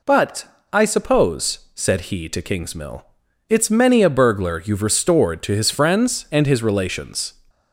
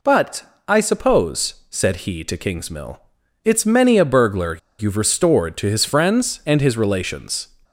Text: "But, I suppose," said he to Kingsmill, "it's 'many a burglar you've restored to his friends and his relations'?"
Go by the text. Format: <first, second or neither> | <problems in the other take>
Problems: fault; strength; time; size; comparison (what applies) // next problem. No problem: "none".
first | pauses between "burglar" and "you've"; slight; at 4.5 s; 0.22 s long